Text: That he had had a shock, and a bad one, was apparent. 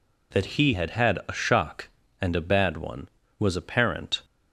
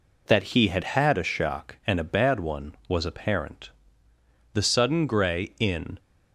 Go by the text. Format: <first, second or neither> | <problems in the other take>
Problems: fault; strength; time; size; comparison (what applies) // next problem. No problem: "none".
first | goes on to say "The sudden grey in"; from 4.5 s on; 1.4 s long